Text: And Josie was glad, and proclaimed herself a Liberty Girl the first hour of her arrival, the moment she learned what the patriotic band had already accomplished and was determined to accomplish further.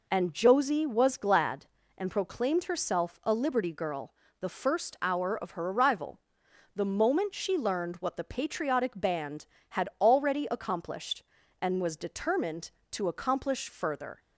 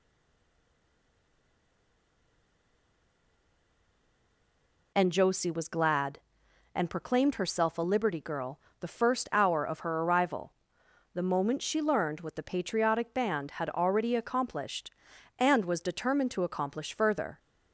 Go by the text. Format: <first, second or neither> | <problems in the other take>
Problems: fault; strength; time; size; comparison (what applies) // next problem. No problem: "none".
first | stays silent before the first word; strong; until 4.9 s; 4.9 s long // pauses between "Girl" and "the"; slight; at 8.5 s; 0.20 s long; slight in the first